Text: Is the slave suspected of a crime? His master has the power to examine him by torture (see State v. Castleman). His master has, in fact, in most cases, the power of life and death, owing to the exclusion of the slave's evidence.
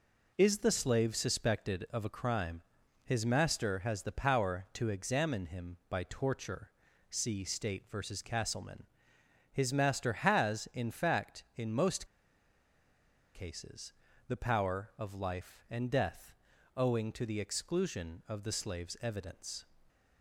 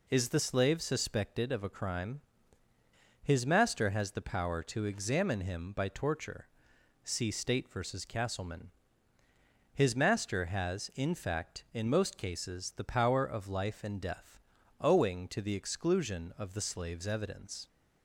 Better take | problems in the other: second | pauses between "most" and "cases"; strong; at 12.0 s; 1.2 s long

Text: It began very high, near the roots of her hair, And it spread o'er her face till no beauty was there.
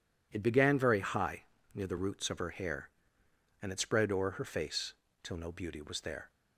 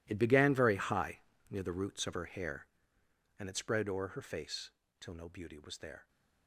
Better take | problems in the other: first | gets quieter; strong; throughout; 16.5 dB // pauses between "face" and "till"; slight; at 4.7 s; 0.28 s long; slight in the first

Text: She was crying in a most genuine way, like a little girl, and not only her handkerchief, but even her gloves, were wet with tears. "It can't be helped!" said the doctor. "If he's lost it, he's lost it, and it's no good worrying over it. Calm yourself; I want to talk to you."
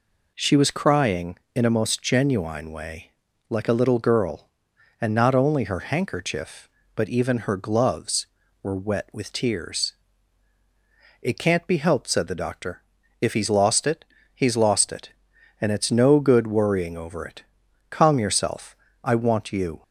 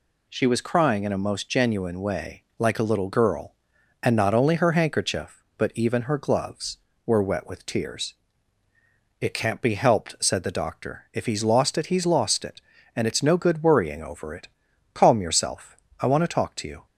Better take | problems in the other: second | skips "to talk to"; at 19.5 s

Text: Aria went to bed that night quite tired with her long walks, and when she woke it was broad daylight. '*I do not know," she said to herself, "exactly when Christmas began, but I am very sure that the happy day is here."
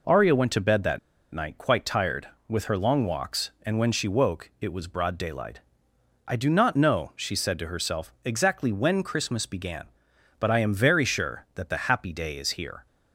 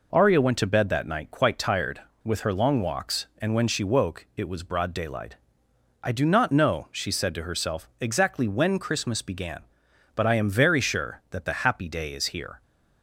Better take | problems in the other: second | pauses between "that" and "night"; slight; at 0.9 s; 0.34 s long

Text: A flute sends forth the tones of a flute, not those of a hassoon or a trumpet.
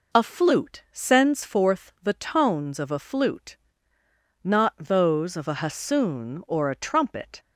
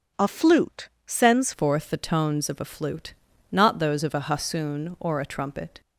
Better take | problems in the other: first | starts louder than the rest; strong; until 1.3 s; 7.5 dB // pauses between "flute" and "sends"; slight; at 0.8 s; 0.18 s long // changes voice at "forth"; from 1.5 s on; 4.3 s long

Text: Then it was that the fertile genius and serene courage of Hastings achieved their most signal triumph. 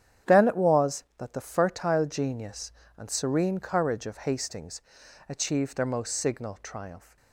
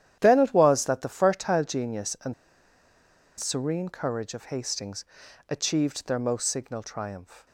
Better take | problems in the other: first | starts louder than the rest; strong; until 1.2 s; 10.5 dB; strong in the first // pauses between "and" and "serene"; at 2.3 s; 1.0 s long // pauses between "Hastings" and "achieved"; at 5.0 s; 0.44 s long; noticeable in the first

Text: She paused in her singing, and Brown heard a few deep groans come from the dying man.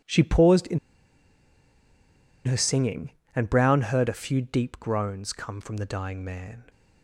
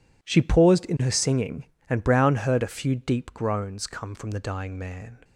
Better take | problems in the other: second | pauses between "in" and "her"; strong; at 0.7 s; 1.6 s long

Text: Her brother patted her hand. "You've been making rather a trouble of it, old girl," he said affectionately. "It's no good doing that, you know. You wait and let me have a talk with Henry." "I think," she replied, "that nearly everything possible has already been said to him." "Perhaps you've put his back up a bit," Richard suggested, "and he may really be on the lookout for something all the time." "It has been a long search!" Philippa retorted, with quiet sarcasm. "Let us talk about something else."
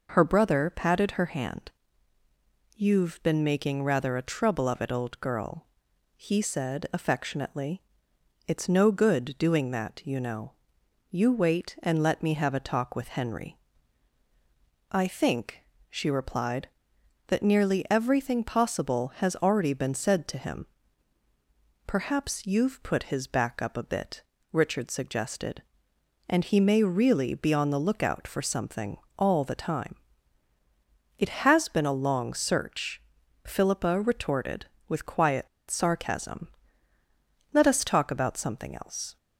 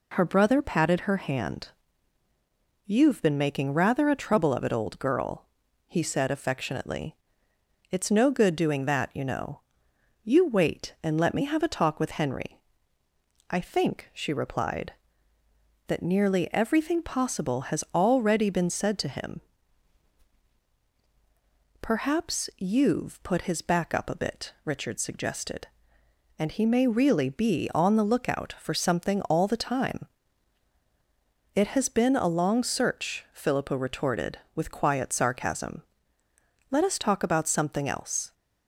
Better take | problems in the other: second | pauses between "something" and "all"; slight; at 28.9 s; 0.18 s long // pauses between "quiet" and "sarcasm"; slight; at 35.4 s; 0.22 s long

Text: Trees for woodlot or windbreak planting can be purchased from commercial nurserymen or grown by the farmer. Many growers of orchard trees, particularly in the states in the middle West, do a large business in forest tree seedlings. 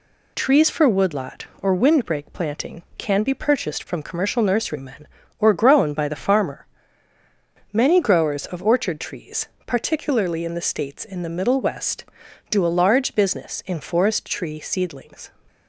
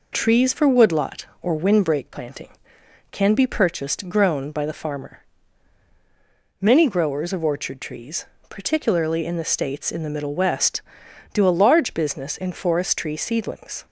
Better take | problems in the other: first | skips "from commercial nurserymen or"; at 4.0 s

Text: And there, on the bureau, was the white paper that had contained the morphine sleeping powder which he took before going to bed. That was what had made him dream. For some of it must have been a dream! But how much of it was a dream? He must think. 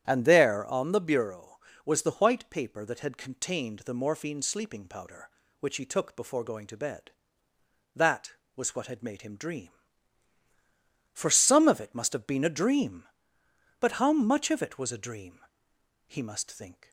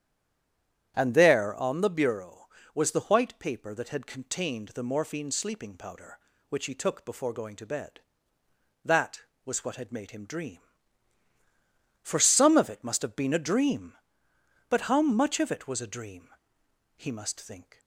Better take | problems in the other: first | stays silent before the first word; slight; until 0.9 s; 0.9 s long // starts louder than the rest; strong; until 1.9 s; 9.5 dB; strong in the first

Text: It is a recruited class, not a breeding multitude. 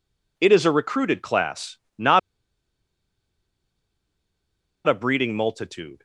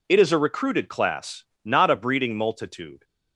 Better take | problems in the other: second | pauses between "not" and "a"; strong; at 2.1 s; 2.6 s long

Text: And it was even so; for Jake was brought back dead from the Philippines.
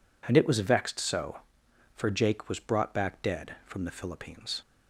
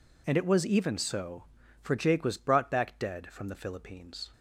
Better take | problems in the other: second | says "vexed" for "even"; at 0.6 s

